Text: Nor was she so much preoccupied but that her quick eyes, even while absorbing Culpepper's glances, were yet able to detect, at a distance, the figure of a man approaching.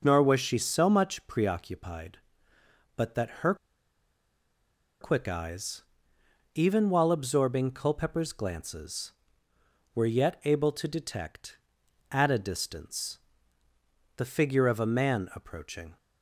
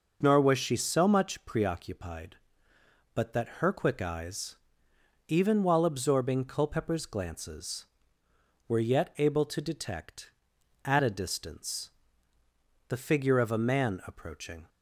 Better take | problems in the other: second | pauses between "her" and "quick"; strong; at 3.5 s; 1.4 s long

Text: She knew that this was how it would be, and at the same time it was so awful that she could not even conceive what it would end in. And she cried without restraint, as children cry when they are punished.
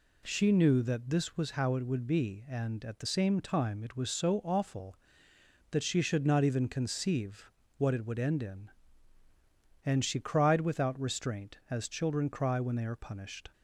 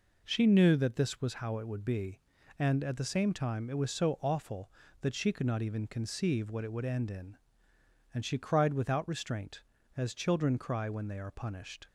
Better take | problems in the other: second | says "should" for "could"; at 6.0 s // pauses between "conceive" and "what"; slight; at 7.5 s; 0.26 s long

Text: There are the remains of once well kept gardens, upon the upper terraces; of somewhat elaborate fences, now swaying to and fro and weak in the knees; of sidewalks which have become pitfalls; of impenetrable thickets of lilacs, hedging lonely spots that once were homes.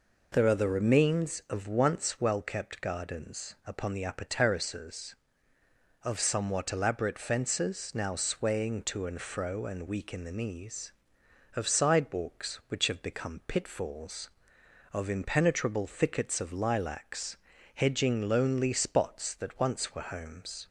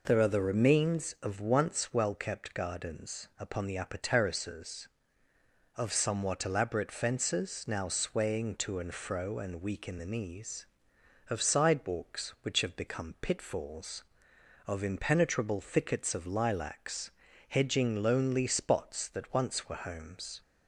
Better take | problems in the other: neither | none

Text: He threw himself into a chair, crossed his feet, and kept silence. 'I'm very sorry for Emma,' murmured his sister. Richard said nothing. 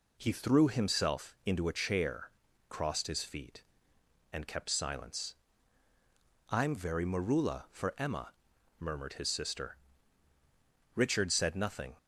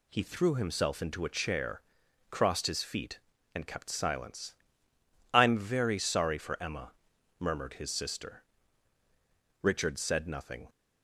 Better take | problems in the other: second | says "marula" for "sorry"; at 7.0 s

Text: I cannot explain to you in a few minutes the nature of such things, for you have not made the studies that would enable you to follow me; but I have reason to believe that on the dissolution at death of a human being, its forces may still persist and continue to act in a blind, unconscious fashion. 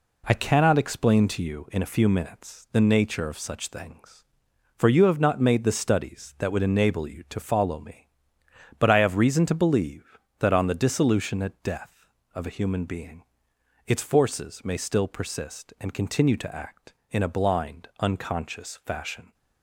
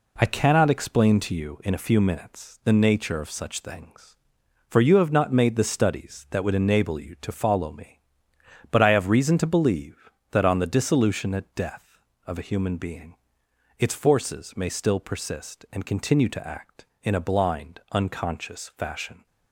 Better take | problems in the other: neither | none

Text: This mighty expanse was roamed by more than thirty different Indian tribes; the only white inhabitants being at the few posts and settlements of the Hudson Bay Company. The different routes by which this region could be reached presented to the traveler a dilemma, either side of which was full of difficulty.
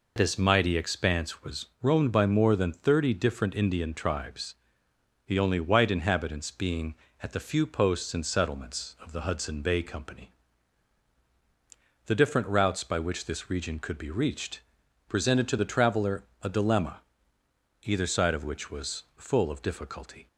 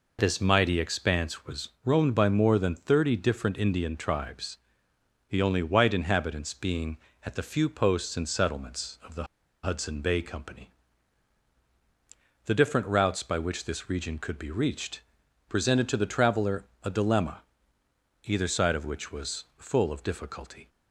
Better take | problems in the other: first | pauses between "was" and "roamed"; slight; at 1.6 s; 0.16 s long; slight in the first // pauses between "the" and "Hudson"; at 9.2 s; 0.39 s long // pauses between "reached" and "presented"; noticeable; at 15.0 s; 0.46 s long; noticeable in the first // pauses between "traveler" and "a"; slight; at 16.6 s; 0.18 s long; slight in the first

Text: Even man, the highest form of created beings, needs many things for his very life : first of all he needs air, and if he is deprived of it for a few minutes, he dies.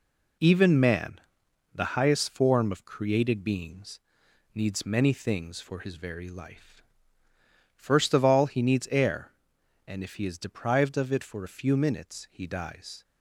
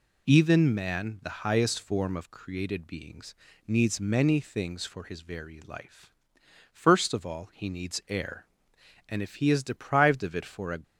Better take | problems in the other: first | stops before "few minutes he dies"; at 10.8 s

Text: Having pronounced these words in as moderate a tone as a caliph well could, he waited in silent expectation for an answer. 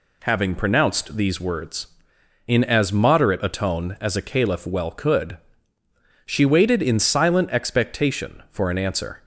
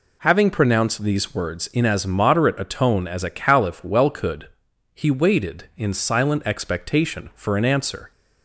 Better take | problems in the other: second | says "she" for "he"; at 6.2 s

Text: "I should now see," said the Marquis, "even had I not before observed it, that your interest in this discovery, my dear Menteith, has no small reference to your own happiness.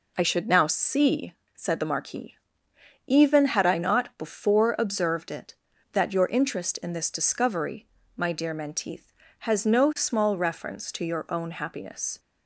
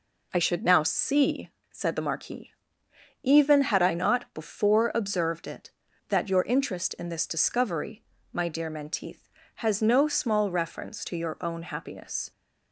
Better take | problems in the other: neither | none

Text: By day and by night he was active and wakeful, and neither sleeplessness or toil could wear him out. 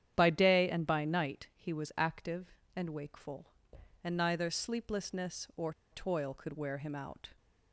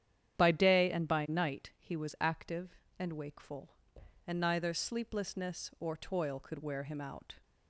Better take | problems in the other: second | starts louder than the rest; strong; until 1.1 s; 9.5 dB; strong in the second // pauses between "or" and "toil"; slight; at 5.7 s; 0.18 s long

